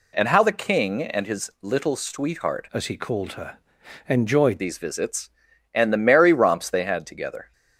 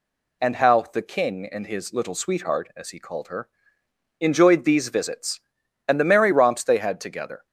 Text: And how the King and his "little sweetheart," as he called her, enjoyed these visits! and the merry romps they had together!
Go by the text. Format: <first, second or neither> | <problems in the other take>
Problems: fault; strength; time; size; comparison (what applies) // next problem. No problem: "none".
second | changes voice from "as" to "enjoyed"; from 2.7 to 4.6 s; 1.9 s long